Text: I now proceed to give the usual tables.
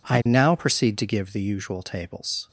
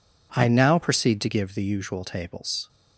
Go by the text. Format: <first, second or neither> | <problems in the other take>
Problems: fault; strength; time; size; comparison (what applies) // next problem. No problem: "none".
neither | none